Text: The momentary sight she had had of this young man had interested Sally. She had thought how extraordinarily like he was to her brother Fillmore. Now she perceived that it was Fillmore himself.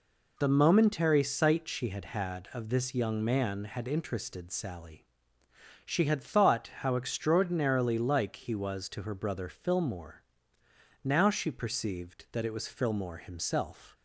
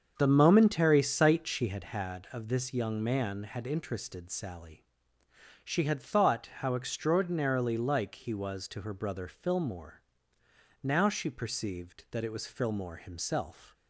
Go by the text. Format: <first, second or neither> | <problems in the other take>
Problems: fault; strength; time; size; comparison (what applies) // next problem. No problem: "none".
first | starts louder than the rest; until 1.9 s; 7 dB